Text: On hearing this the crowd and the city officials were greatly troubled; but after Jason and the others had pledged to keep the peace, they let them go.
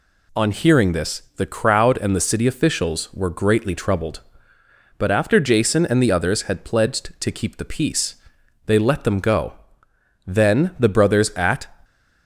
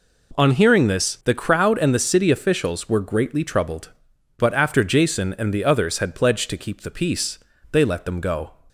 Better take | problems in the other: second | goes on to say "Then the brothers at"; from 10.2 s on; 1.3 s long

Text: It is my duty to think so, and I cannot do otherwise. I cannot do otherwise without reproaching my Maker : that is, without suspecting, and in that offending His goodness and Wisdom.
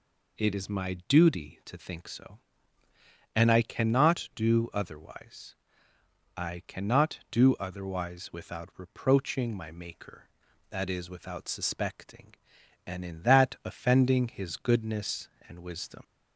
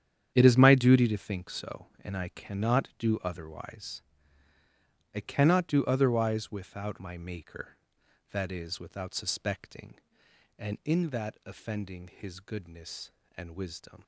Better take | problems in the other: first | starts louder than the rest; strong; until 1.3 s; 9 dB // skips "reproaching"; at 6.9 s

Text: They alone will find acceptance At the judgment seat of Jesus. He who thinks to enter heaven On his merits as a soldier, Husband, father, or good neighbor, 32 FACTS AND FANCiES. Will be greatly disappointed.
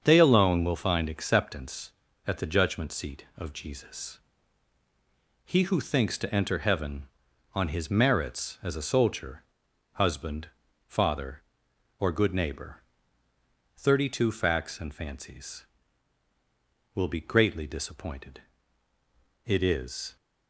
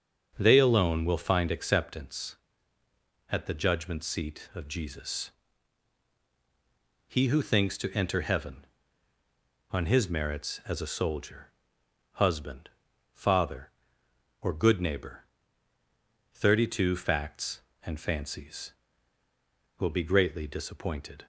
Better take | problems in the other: second | starts louder than the rest; until 1.0 s; 7 dB; also in the second // goes on to say "It is"; noticeable; from 19.4 s on; 0.70 s long

